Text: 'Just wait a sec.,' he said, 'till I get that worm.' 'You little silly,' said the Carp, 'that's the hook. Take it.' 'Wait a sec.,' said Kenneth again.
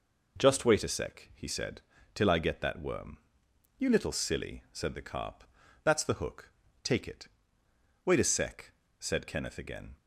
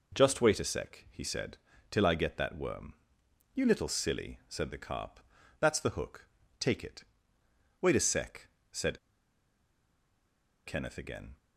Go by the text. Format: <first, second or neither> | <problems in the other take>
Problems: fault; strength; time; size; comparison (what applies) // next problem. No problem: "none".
first | pauses between "said" and "Kenneth"; strong; at 8.9 s; 1.6 s long